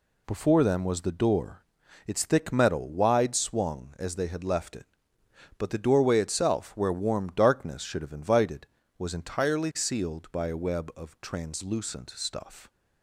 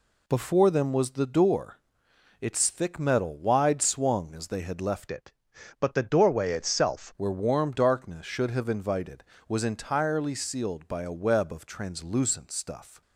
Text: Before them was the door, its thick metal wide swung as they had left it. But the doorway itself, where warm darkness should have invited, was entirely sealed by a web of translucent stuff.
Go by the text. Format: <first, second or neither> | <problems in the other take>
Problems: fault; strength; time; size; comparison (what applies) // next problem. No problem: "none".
first | changes voice from "it" to "itself"; from 5.1 to 7.1 s; 2.0 s long